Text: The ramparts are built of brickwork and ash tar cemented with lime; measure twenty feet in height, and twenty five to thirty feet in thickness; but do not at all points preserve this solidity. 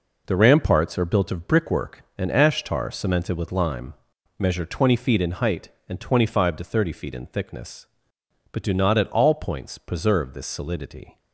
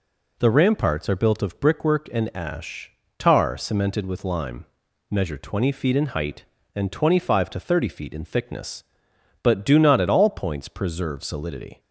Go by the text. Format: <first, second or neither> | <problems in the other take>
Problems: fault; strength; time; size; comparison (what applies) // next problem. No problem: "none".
first | pauses between "ash" and "tar"; slight; at 2.9 s; 0.26 s long // skips "this"; at 11.2 s